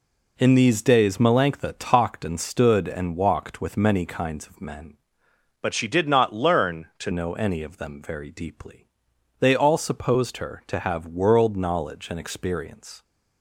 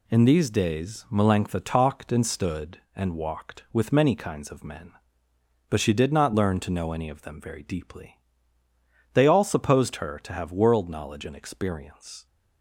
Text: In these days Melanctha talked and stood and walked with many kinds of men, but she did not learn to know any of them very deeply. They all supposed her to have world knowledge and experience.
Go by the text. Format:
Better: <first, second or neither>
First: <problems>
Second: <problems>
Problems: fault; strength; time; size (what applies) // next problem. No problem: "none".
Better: second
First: changes voice from "but" to "to"; from 5.6 to 7.1 s; 1.5 s long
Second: none